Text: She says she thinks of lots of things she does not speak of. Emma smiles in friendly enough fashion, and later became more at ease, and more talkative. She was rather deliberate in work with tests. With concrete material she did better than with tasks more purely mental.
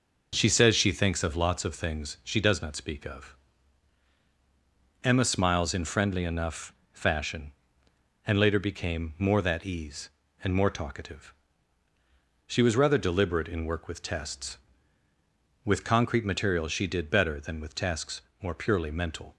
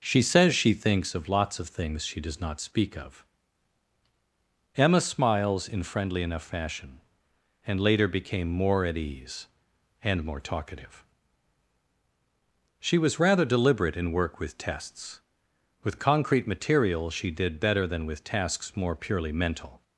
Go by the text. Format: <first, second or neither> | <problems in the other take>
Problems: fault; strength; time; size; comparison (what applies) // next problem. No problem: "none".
second | pauses between "enough" and "fashion"; slight; at 6.7 s; 0.18 s long // says "that" for "at"; at 9.4 s // pauses between "tasks" and "more"; slight; at 18.2 s; 0.20 s long